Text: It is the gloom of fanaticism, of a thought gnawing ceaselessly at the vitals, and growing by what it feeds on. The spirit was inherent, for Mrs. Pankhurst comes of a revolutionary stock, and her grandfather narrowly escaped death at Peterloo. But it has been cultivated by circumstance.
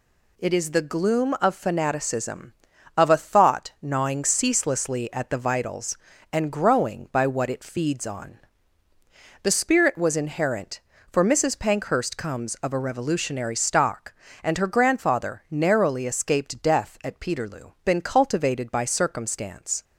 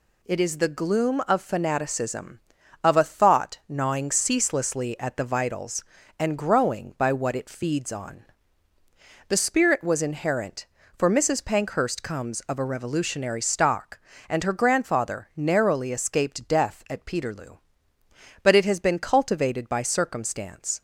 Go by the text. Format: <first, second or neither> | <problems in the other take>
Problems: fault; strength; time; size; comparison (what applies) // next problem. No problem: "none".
second | skips "But it has"; at 17.7 s